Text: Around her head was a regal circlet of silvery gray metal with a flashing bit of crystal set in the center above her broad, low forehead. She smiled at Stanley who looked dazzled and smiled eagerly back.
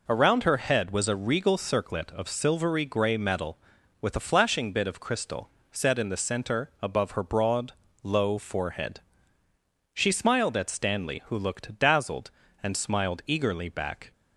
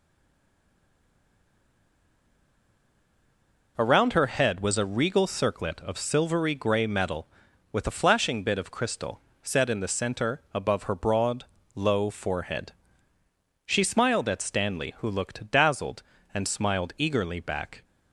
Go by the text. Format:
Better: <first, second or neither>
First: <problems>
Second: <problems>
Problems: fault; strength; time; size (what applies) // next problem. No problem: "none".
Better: first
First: pauses between "crystal" and "set"; slight; at 5.4 s; 0.22 s long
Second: stays silent before the first word; strong; until 3.7 s; 3.7 s long // pauses between "crystal" and "set"; slight; at 9.2 s; 0.22 s long